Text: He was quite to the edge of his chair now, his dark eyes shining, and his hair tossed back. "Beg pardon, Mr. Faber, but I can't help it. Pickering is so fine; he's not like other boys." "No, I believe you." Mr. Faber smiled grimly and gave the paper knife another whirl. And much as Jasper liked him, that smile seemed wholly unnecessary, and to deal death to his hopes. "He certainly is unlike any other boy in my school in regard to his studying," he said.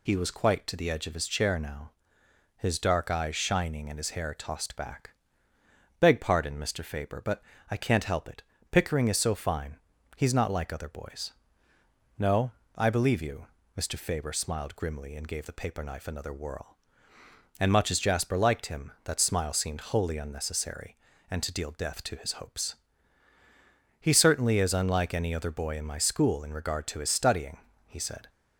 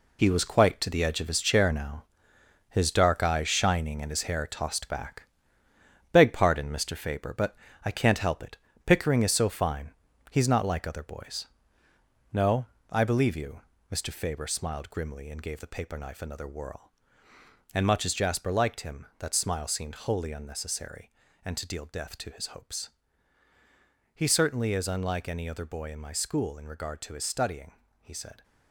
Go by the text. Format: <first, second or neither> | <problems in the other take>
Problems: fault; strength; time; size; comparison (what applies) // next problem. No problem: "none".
first | gets quieter; strong; throughout; 8.5 dB // pauses between "but" and "I"; slight; at 7.5 s; 0.30 s long; slight in the first